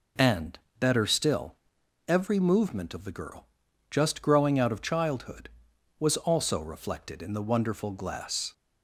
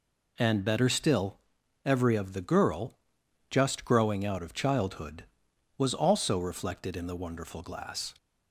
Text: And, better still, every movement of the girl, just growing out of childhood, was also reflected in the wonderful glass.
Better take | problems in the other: first | skips "movement"; at 2.1 s

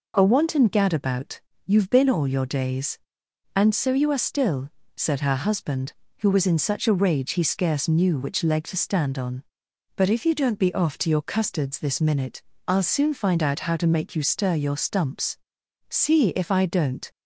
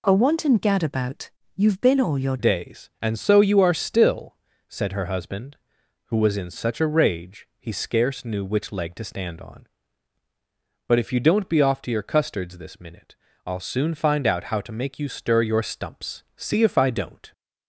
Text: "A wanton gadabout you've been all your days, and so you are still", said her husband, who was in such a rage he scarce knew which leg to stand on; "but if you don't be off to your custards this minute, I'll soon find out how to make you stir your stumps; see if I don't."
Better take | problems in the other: first | pauses between "gadabout" and "you've"; slight; at 1.3 s; 0.24 s long; slight in the first // changes voice at "days"; from 2.3 s on; 15.0 s long

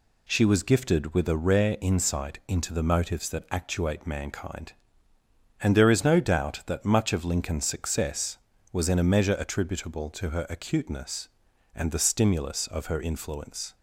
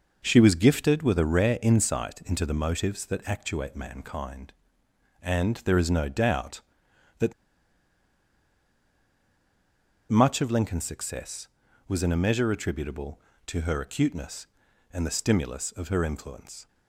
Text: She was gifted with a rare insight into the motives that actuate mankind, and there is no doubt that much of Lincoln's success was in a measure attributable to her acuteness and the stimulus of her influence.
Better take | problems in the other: first | pauses between "that" and "much"; strong; at 7.3 s; 2.7 s long

